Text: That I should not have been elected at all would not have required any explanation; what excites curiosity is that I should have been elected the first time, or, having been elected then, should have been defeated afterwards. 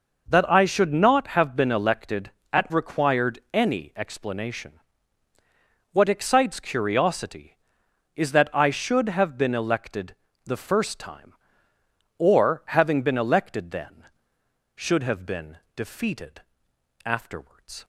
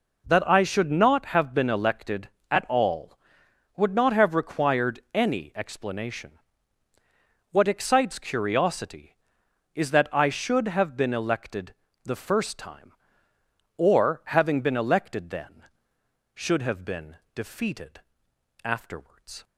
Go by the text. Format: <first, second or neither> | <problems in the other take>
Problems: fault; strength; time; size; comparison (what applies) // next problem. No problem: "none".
second | skips "all would not have"; at 2.6 s // pauses between "elected" and "the"; slight; at 10.1 s; 0.30 s long; slight in the second // pauses between "been" and "defeated"; slight; at 15.5 s; 0.18 s long; slight in the second // pauses between "defeated" and "afterwards"; noticeable; at 16.3 s; 0.66 s long; noticeable in the second